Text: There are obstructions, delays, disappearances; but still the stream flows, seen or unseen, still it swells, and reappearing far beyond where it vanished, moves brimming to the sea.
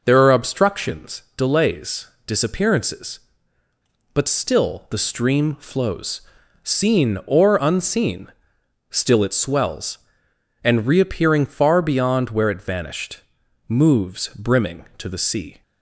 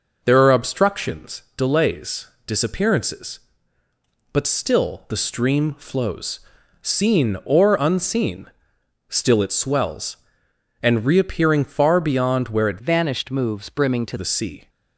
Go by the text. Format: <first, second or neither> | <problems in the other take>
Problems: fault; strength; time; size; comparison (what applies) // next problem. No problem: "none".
first | changes voice from "vanished" to "to"; from 12.8 to 14.1 s; 1.3 s long